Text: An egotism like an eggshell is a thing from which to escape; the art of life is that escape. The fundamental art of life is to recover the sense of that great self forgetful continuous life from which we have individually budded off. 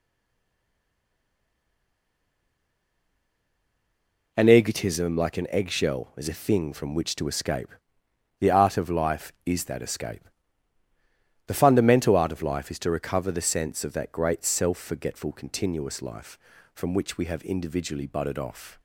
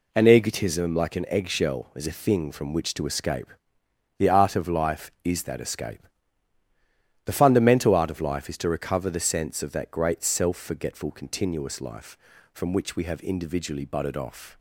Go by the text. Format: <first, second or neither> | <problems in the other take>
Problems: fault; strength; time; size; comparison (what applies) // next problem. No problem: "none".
second | stays silent before the first word; strong; until 4.3 s; 4.3 s long